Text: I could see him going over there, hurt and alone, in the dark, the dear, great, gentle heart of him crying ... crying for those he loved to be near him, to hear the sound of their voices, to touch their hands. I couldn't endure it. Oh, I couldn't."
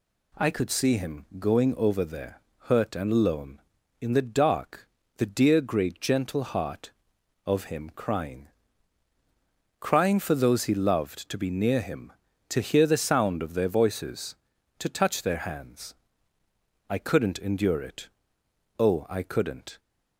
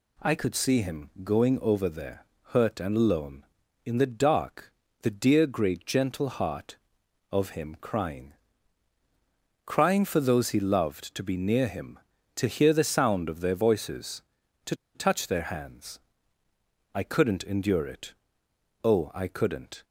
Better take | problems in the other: first | pauses between "to" and "touch"; slight; at 14.7 s; 0.21 s long

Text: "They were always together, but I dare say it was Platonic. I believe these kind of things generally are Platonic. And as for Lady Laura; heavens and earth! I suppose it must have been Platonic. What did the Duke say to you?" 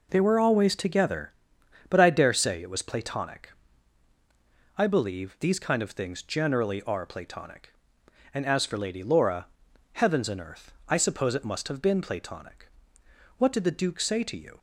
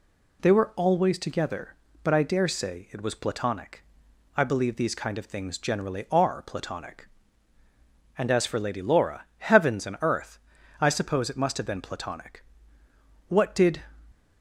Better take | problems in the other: first | stops before "the Duke say to you"; at 14.1 s

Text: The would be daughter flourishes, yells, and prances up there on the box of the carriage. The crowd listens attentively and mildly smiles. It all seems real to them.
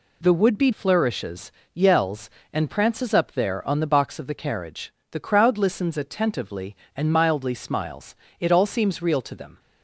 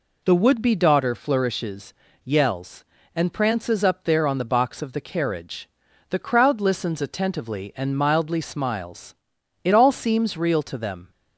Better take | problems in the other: second | skips "daughter"; at 0.7 s

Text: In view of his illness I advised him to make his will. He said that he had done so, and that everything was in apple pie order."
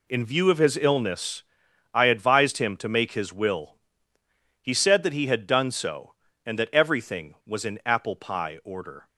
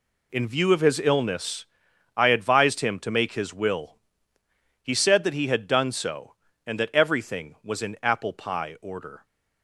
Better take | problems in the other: neither | pauses between "illness" and "I"; noticeable; the same in both

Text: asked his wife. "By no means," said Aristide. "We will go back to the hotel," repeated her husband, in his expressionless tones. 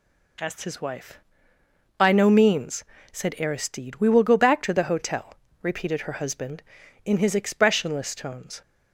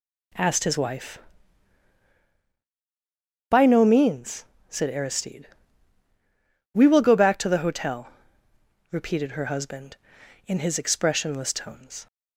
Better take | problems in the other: neither | none

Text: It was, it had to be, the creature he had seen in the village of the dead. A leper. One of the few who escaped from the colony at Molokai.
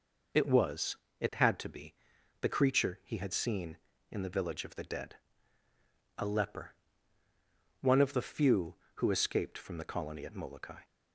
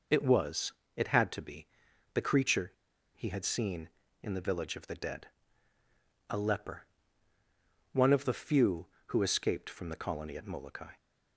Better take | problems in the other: first | pauses between "creature" and "he"; at 2.7 s; 0.42 s long

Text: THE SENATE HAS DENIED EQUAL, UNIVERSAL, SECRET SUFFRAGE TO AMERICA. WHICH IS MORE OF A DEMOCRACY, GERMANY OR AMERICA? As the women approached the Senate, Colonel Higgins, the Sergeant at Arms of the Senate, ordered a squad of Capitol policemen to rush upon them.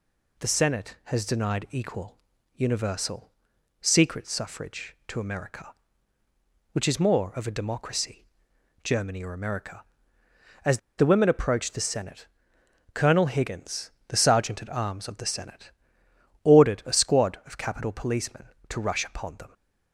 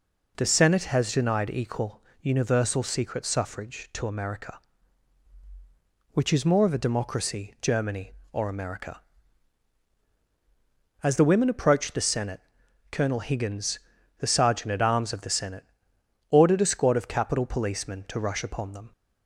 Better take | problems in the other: second | pauses between "As" and "the"; slight; at 10.7 s; 0.19 s long

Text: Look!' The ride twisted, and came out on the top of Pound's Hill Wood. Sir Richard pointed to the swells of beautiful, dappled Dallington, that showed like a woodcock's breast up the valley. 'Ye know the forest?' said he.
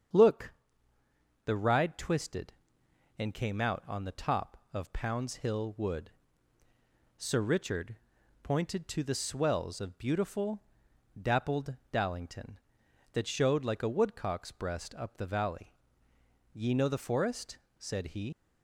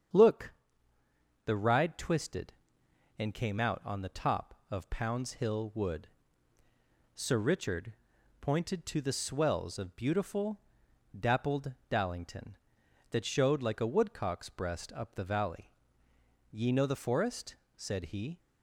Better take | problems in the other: second | starts louder than the rest; strong; until 2.0 s; 7.5 dB; strong in the second // pauses between "Richard" and "pointed"; noticeable; at 7.9 s; 0.47 s long; noticeable in the second // pauses between "dappled" and "Dallington"; slight; at 11.7 s; 0.18 s long; slight in the second // leaves "he" unfinished; at 18.3 s; 85 ms

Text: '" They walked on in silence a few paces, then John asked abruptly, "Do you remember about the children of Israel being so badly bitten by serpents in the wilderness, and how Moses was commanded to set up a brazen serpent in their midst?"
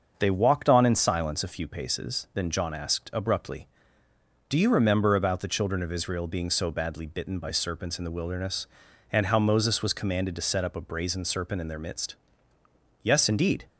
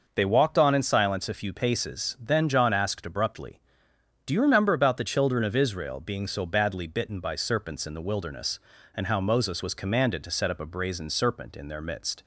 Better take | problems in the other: second | starts louder than the rest; until 1.1 s; 6.5 dB // goes on to say "Yes indeed"; noticeable; from 13.0 s on; 0.62 s long

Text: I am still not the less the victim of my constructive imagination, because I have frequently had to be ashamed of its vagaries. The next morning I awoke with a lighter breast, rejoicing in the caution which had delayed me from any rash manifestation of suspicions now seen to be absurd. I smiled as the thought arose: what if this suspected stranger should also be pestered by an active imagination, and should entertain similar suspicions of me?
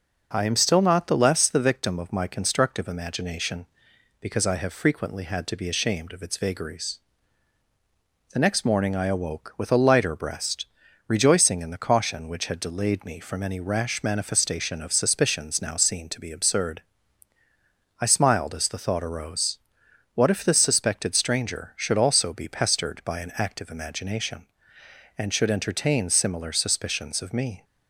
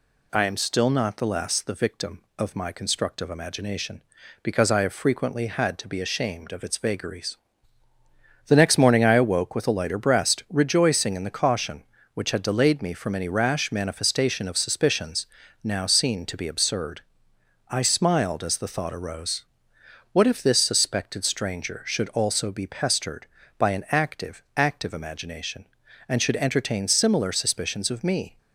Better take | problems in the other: first | pauses between "suspicions" and "now"; at 15.2 s; 0.38 s long // says "active" twice; at 24.5 s

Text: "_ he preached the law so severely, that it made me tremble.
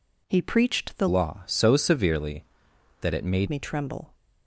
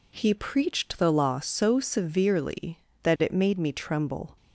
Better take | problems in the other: second | changes voice from "law" to "made"; from 1.0 to 3.4 s; 2.4 s long

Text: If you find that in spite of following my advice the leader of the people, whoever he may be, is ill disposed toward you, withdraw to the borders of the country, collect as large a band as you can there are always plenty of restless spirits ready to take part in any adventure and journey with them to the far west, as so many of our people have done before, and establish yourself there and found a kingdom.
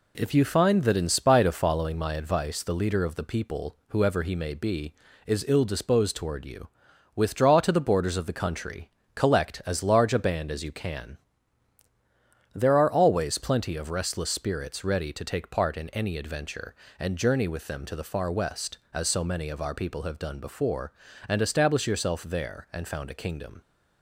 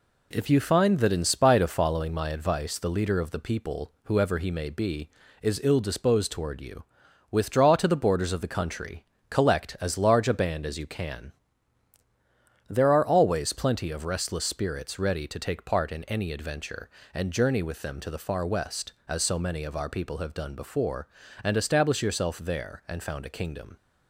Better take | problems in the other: neither | pauses between "can" and "there"; strong; the same in both

